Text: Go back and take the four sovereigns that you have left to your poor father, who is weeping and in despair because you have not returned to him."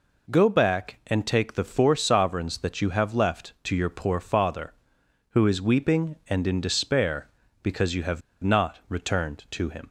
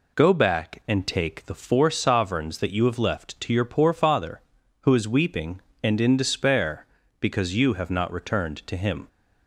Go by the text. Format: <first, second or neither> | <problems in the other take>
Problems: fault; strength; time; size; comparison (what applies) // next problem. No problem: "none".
second | pauses between "have" and "not"; slight; at 8.2 s; 0.23 s long